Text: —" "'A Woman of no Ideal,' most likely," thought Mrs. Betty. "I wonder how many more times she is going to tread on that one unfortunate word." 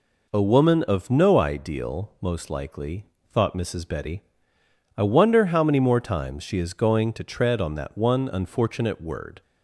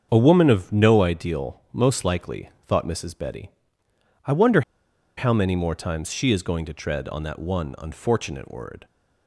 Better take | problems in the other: first | starts louder than the rest; strong; until 1.1 s; 7 dB // pauses between "wonder" and "how"; noticeable; at 4.6 s; 0.55 s long

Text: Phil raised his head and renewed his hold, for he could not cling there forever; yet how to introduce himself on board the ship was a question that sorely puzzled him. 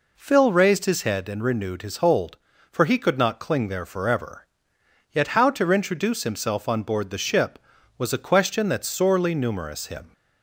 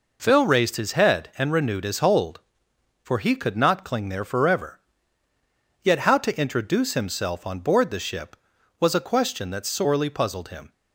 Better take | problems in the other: second | says "numerous" for "puzzled"; at 9.3 s

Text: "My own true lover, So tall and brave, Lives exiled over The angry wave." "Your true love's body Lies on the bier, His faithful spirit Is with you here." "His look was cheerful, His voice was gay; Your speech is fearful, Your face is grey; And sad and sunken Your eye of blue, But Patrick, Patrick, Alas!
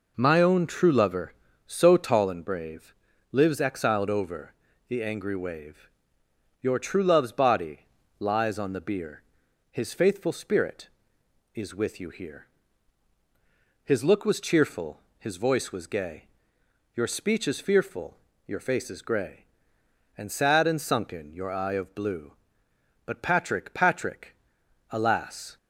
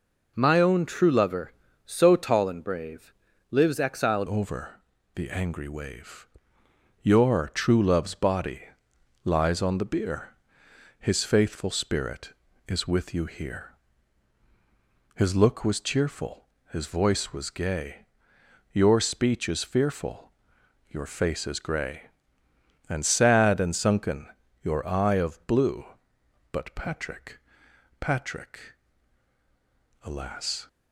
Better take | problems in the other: first | changes voice at "over"; from 4.2 s on; 26.4 s long // pauses between "over" and "The"; slight; at 4.8 s; 0.32 s long; slight in the first // pauses between "body" and "Lies"; noticeable; at 8.6 s; 0.58 s long; slight in the first // pauses between "sunken" and "Your"; slight; at 24.2 s; 0.34 s long

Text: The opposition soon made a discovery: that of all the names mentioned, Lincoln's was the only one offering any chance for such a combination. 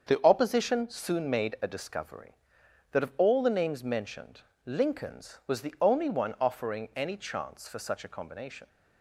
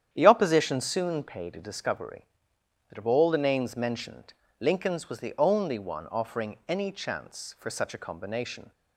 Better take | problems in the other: first | starts louder than the rest; strong; until 1.1 s; 9.5 dB; also in the first // says "paid" for "made"; at 1.2 s

